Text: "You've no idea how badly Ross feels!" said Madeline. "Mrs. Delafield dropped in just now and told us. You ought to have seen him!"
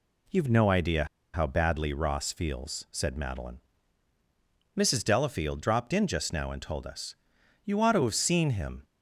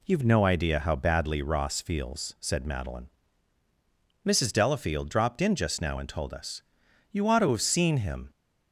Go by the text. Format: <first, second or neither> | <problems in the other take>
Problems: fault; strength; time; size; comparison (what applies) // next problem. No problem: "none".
second | pauses between "idea" and "how"; slight; at 1.0 s; 0.28 s long